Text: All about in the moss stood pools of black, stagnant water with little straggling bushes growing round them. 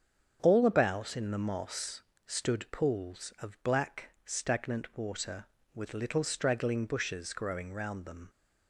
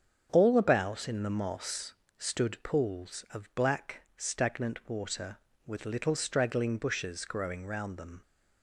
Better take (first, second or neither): neither